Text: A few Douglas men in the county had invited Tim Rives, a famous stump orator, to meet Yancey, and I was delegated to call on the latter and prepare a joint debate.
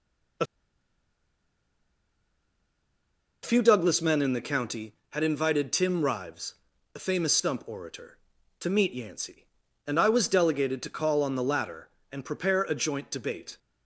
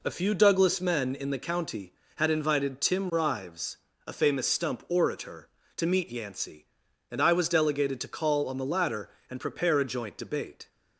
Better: second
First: pauses between "A" and "few"; strong; at 0.4 s; 2.9 s long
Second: none

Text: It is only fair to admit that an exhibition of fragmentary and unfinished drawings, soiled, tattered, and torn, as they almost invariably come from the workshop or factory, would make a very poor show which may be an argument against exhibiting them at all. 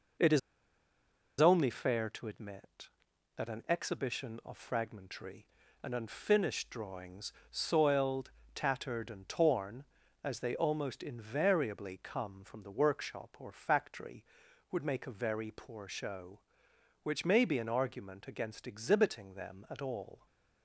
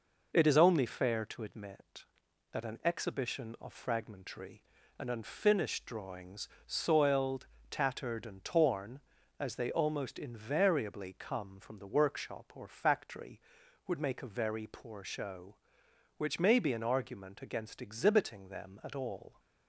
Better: second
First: pauses between "is" and "only"; at 0.3 s; 0.99 s long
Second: none

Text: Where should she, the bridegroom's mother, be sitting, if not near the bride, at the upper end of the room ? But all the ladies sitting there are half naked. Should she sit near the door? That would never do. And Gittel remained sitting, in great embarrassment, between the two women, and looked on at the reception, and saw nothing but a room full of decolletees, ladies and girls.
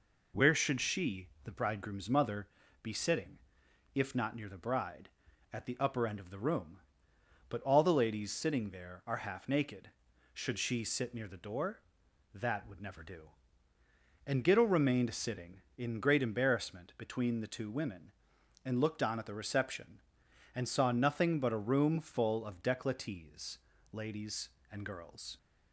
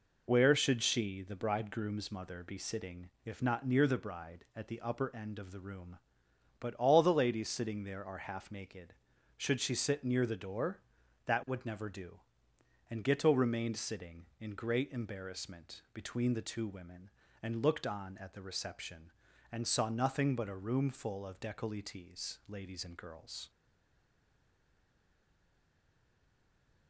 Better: first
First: none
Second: stays silent after the last word; strong; from 23.4 s on; 3.4 s long

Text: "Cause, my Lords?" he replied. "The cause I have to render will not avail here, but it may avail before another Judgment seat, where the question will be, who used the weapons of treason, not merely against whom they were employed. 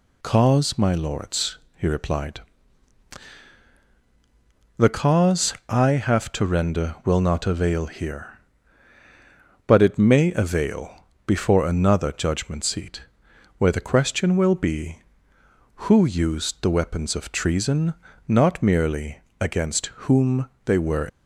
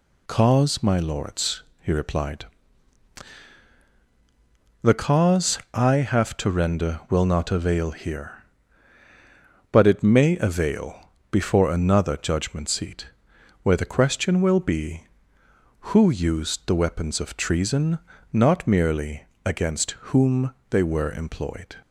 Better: second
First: pauses between "cause" and "I"; slight; at 5.5 s; 0.16 s long // pauses between "avail" and "before"; slight; at 11.0 s; 0.20 s long // pauses between "merely" and "against"; slight; at 19.2 s; 0.18 s long // pauses between "against" and "whom"; slight; at 19.8 s; 0.16 s long // pauses between "whom" and "they"; slight; at 20.4 s; 0.16 s long // stops before "employed"; at 21.0 s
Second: pauses between "cause" and "I"; slight; at 5.5 s; 0.16 s long // pauses between "avail" and "before"; slight; at 11.0 s; 0.20 s long // pauses between "merely" and "against"; slight; at 19.2 s; 0.18 s long // pauses between "against" and "whom"; slight; at 19.9 s; 0.16 s long // pauses between "whom" and "they"; slight; at 20.5 s; 0.16 s long

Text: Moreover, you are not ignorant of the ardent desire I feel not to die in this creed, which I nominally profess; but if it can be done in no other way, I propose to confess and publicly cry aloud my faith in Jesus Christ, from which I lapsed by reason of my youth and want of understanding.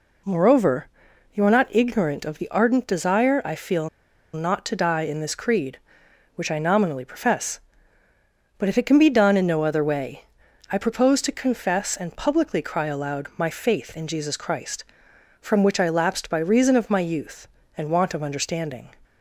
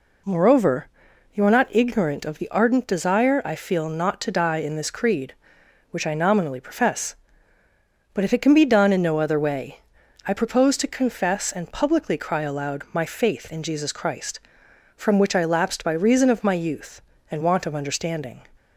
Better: second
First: pauses between "feel" and "not"; at 3.8 s; 0.45 s long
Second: none

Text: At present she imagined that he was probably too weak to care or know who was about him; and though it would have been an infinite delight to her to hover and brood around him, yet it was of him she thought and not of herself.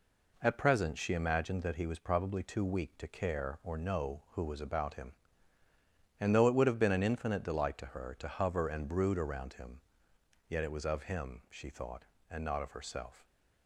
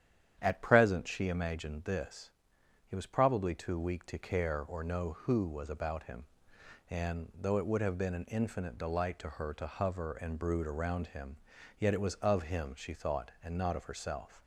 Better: first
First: none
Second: starts louder than the rest; strong; until 1.4 s; 9.5 dB // says "this" for "that"; at 1.8 s

